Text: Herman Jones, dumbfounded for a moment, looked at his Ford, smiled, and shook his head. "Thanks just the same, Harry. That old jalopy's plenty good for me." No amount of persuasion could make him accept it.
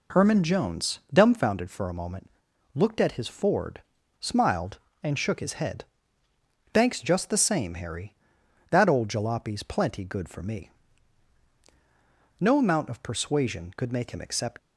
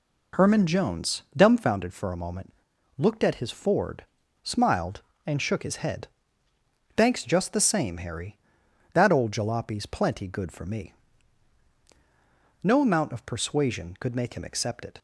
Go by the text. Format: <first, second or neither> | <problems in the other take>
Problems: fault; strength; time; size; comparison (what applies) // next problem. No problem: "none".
second | stops before "it"; at 14.5 s